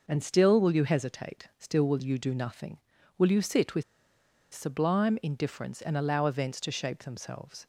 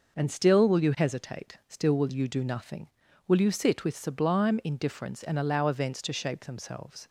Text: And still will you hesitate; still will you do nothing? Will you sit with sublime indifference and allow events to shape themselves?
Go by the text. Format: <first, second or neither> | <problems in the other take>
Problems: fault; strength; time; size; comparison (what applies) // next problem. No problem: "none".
second | pauses between "with" and "sublime"; noticeable; at 3.8 s; 0.70 s long